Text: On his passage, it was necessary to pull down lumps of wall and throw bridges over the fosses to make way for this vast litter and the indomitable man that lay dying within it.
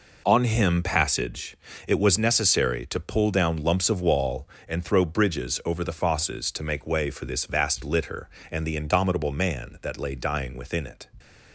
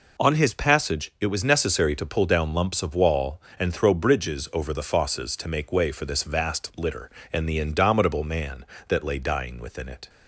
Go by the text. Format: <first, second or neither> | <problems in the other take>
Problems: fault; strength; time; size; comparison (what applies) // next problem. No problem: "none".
second | says "him" for "his"; at 0.4 s